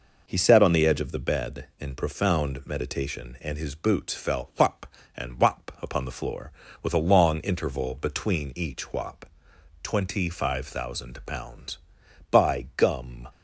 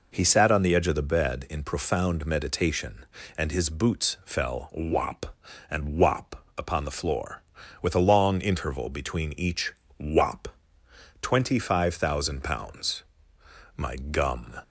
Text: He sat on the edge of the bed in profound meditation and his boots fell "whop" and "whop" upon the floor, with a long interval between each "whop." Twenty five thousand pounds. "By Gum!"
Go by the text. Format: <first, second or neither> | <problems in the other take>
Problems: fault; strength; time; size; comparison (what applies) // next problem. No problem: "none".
first | pauses between "each" and "whop"; slight; at 9.7 s; 0.26 s long // says "My" for "By"; at 13.7 s